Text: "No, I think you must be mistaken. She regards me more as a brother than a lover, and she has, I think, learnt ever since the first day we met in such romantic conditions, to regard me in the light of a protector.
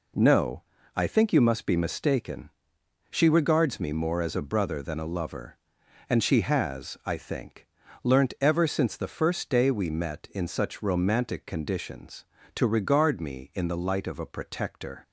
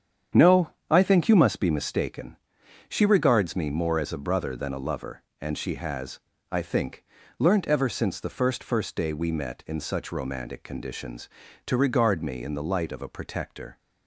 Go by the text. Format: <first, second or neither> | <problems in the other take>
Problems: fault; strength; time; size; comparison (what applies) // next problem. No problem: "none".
first | starts louder than the rest; strong; until 1.5 s; 8.5 dB // says "first" twice; at 8.6 s